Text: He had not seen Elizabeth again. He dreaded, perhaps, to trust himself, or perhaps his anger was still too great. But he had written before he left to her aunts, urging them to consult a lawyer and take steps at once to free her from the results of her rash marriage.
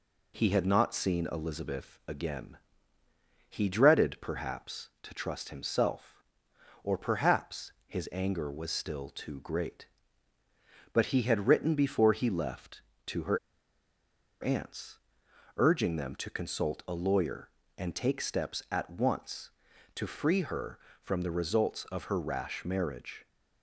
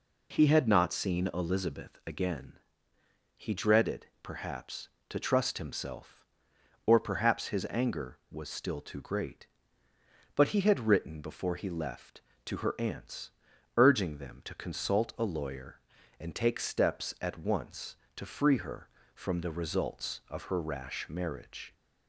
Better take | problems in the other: second | pauses between "perhaps" and "his"; slight; at 7.7 s; 0.16 s long // pauses between "her" and "aunts"; at 13.3 s; 1.0 s long

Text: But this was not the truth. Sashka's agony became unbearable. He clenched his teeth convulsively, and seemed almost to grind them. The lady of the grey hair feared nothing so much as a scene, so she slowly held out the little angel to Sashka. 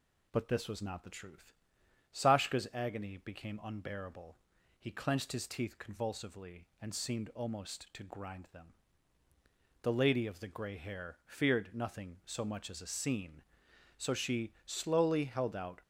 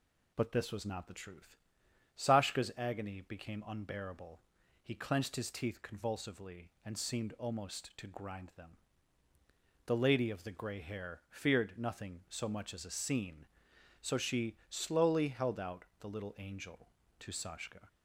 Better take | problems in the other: second | stops before "the little angel to Sashka"; at 15.8 s

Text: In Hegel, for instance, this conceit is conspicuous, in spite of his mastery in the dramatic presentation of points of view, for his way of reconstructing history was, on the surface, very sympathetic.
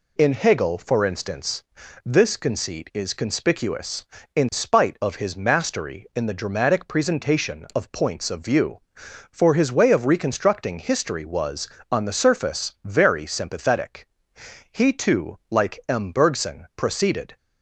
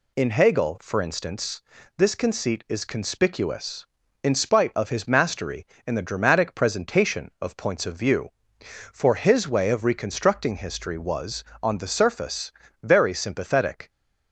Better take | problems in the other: second | goes on to say "He too like M Bergson proceeded"; strong; from 14.7 s on; 2.6 s long

